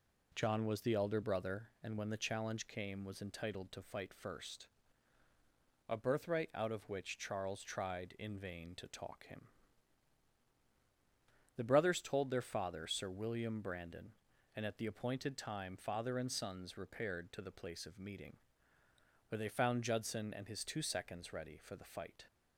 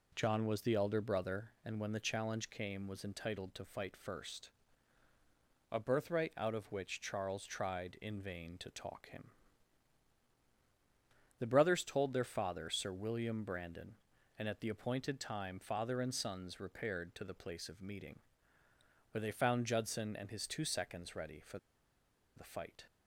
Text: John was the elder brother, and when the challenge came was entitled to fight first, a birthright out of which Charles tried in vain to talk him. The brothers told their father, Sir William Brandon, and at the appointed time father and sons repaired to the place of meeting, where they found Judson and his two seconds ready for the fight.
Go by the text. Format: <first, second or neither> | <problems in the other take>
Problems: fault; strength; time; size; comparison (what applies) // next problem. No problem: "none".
first | pauses between "for" and "the"; noticeable; at 21.5 s; 0.78 s long